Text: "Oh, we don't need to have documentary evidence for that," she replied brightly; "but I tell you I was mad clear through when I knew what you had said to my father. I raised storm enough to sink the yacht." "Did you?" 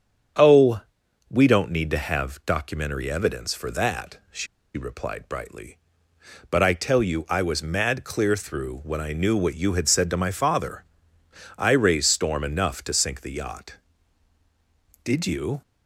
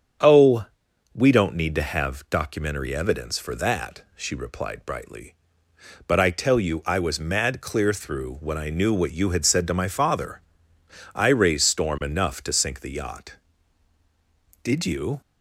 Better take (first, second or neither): second